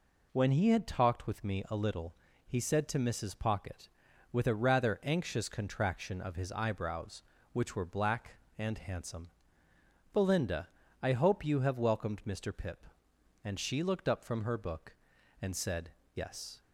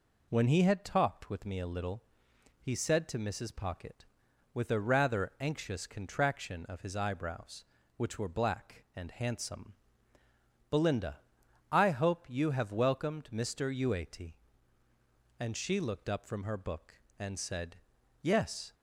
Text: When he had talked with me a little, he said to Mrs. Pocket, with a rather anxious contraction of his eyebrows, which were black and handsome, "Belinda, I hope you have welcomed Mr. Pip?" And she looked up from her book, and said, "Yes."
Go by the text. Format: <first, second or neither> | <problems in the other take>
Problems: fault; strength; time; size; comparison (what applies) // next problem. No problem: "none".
first | says "Uate" for "Pip"; at 13.7 s